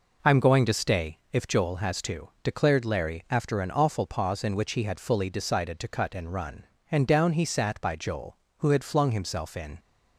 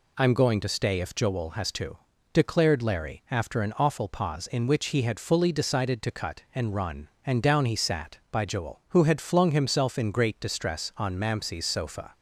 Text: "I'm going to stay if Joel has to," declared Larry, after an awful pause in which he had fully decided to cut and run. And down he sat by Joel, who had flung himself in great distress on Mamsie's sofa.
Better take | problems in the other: second | stops before "great distress on Mamsie's sofa"; at 9.7 s

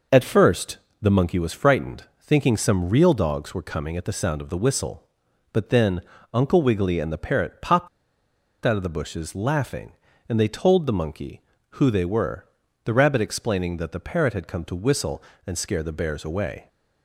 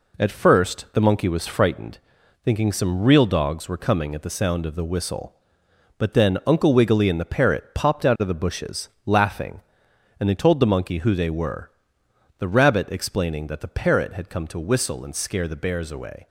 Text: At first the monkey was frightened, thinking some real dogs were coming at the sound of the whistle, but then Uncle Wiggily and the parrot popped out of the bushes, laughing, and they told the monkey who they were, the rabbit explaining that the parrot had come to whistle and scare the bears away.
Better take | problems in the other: second | pauses between "first" and "the"; slight; at 0.7 s; 0.20 s long // pauses between "then" and "Uncle"; slight; at 6.0 s; 0.32 s long // pauses between "popped" and "out"; noticeable; at 7.8 s; 0.77 s long

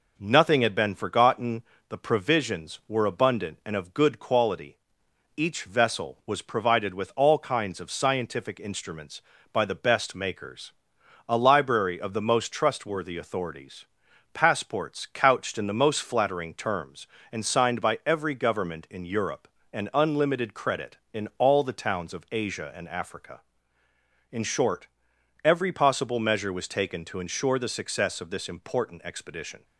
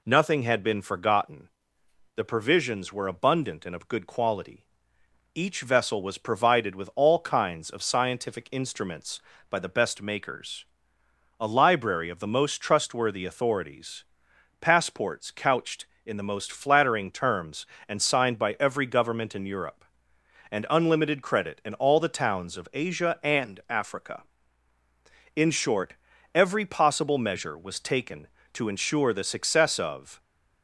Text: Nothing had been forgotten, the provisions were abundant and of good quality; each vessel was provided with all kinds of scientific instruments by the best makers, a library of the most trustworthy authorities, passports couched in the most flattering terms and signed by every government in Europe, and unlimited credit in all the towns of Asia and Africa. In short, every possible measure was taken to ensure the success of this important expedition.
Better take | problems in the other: first | stops before "this important expedition"; at 30.2 s

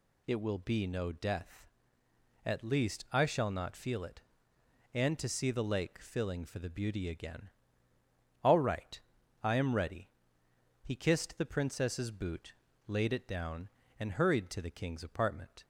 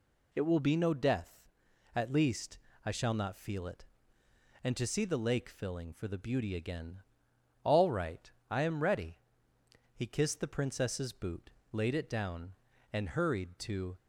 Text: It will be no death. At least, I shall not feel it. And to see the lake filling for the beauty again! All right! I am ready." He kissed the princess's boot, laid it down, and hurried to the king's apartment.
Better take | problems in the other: first | stops before "the king's apartment"; at 13.9 s

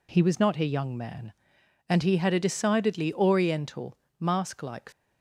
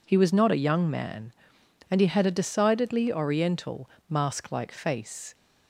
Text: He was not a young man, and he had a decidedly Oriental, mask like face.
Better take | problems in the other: second | stops before "face"; at 4.9 s

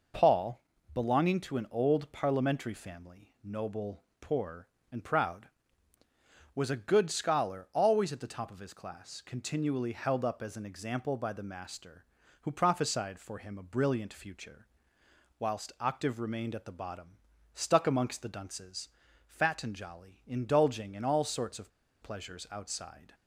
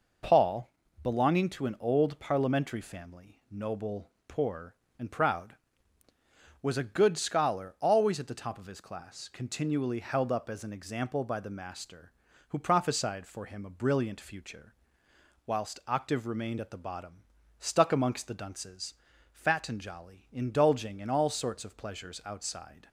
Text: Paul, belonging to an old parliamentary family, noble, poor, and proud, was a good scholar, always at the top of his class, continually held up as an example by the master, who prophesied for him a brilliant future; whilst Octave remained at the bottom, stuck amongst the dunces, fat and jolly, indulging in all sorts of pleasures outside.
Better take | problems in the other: second | pauses between "of" and "pleasures"; slight; at 21.7 s; 0.34 s long

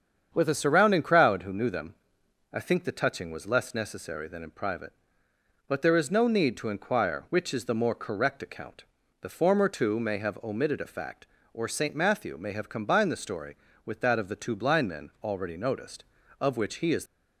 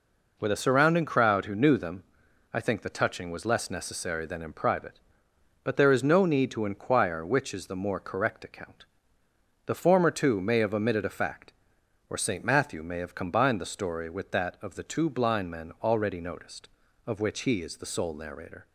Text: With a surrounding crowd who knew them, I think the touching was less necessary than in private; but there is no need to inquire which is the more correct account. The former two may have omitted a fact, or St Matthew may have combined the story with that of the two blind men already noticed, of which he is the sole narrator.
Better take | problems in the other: second | starts louder than the rest; strong; until 1.3 s; 8 dB // stops before "the sole narrator"; at 17.0 s

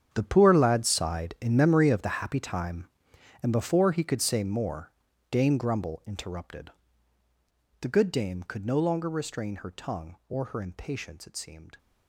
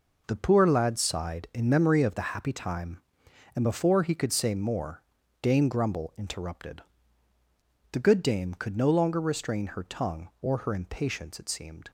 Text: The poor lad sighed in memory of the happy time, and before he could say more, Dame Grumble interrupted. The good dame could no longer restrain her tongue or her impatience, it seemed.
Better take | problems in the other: second | gets quieter; strong; throughout; 15 dB

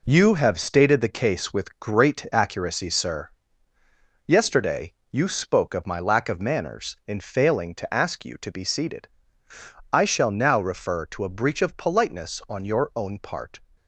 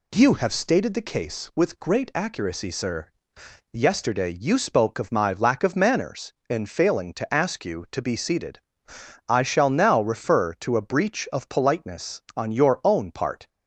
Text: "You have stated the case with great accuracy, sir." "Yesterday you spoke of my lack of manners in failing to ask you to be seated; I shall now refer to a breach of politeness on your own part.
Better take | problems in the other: second | gets quieter; strong; throughout; 7 dB // pauses between "Yesterday" and "you"; slight; at 4.9 s; 0.18 s long

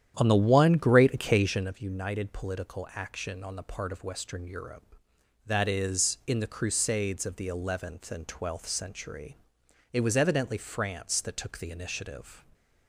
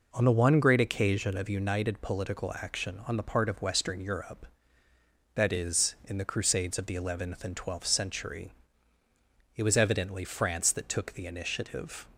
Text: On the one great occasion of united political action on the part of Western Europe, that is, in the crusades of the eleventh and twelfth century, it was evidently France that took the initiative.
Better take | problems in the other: second | starts louder than the rest; strong; until 1.8 s; 10 dB

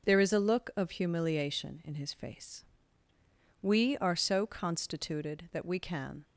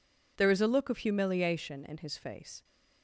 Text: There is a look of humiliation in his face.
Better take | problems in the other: second | starts louder than the rest; noticeable; until 1.1 s; 6 dB // goes on to say "We are so constituted that we can"; strong; from 3.6 s on; 2.6 s long

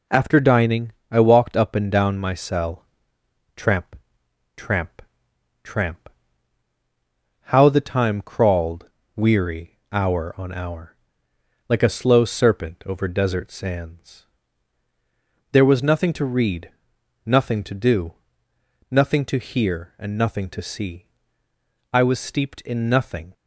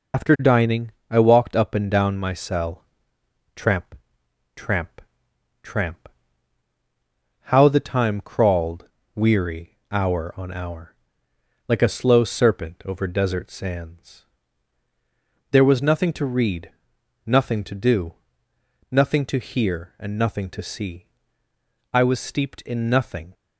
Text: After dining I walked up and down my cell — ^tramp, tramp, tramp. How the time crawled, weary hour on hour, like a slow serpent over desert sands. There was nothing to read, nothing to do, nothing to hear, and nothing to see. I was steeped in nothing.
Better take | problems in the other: first | loses the start of "After"; at 0.1 s; 85 ms // pauses between "dining" and "I"; slight; at 0.9 s; 0.18 s long; slight in the first

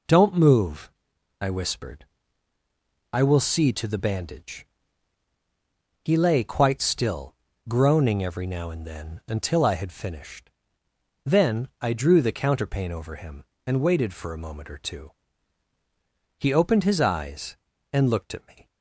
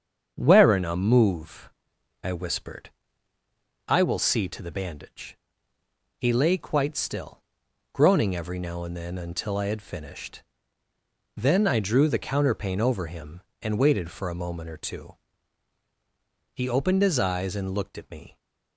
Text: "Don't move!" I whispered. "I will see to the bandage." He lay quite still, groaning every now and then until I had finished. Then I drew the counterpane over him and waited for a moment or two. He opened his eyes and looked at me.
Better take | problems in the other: first | starts louder than the rest; strong; until 1.3 s; 7.5 dB // says "Werena" for "Don't"; at 0.3 s

